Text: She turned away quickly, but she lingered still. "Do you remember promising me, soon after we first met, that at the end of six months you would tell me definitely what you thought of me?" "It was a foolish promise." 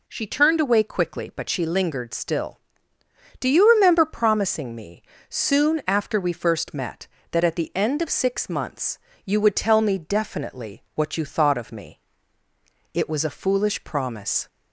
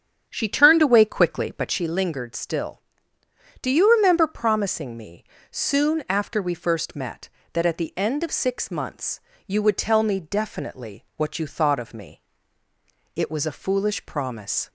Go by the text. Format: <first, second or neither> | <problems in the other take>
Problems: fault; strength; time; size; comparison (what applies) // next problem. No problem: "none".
first | starts louder than the rest; strong; until 1.8 s; 8.5 dB // pauses between "months" and "you"; slight; at 9.1 s; 0.28 s long; slight in the first